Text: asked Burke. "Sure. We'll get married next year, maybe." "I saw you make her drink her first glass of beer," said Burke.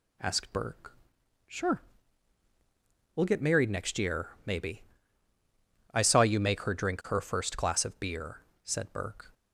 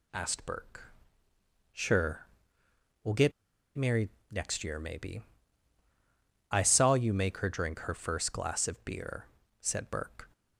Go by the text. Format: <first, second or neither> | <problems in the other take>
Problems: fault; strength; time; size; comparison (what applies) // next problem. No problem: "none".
first | pauses between "get" and "married"; at 3.3 s; 0.45 s long // pauses between "married" and "next"; slight; at 4.0 s; 0.22 s long